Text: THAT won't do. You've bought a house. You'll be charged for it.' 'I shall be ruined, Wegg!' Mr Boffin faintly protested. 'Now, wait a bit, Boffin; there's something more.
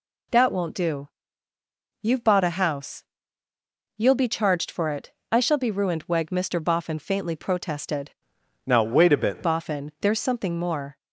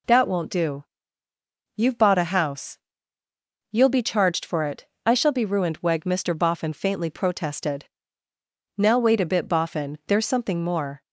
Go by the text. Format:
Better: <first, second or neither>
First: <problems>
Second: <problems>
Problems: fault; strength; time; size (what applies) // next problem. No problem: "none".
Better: second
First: changes voice from "Now" to "bit"; from 8.6 to 9.4 s; 0.8 s long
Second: none